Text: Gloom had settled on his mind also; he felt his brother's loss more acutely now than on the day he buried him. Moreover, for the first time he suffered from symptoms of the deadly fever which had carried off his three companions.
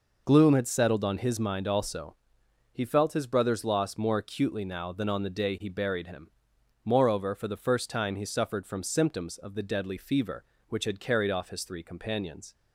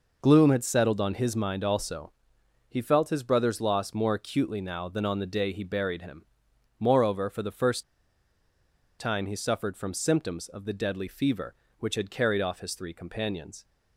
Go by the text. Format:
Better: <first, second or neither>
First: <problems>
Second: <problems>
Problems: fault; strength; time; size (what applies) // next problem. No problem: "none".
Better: first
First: none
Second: pauses between "first" and "time"; at 7.8 s; 1.1 s long